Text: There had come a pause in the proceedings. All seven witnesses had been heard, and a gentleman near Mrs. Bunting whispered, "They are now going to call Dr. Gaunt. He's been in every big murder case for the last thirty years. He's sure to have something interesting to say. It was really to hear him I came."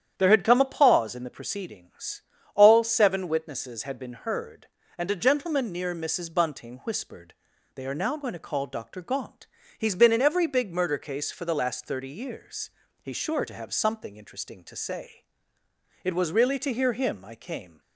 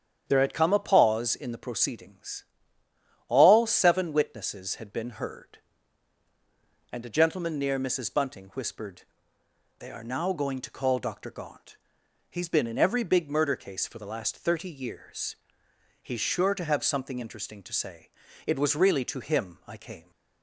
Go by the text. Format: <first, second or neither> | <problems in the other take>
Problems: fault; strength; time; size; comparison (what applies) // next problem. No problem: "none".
first | starts louder than the rest; strong; until 1.2 s; 8.5 dB; strong in the first // skips "hear"; at 19.2 s